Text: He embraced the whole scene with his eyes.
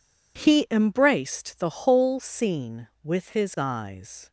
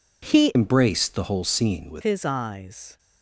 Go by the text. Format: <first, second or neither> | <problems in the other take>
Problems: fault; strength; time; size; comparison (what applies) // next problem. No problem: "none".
first | changes voice from "embraced" to "with"; from 0.5 to 2.0 s; 1.5 s long